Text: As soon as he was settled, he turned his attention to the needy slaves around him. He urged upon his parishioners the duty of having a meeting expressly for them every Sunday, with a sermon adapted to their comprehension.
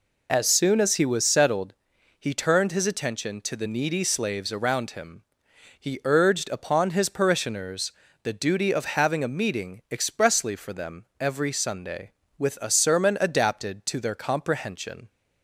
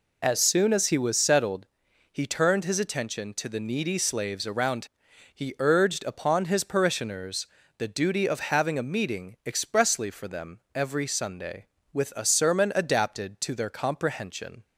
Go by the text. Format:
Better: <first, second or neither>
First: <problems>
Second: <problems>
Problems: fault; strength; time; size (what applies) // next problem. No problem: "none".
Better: first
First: pauses between "parishioners" and "the"; slight; at 7.9 s; 0.30 s long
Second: skips "him"; at 5.0 s // pauses between "parishioners" and "the"; slight; at 7.4 s; 0.30 s long